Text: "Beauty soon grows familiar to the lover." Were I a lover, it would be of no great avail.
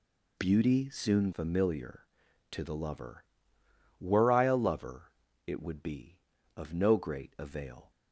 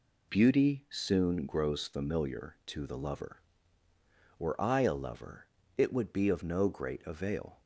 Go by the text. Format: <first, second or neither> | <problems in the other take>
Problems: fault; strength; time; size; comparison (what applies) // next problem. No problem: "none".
second | skips "grows"; at 1.3 s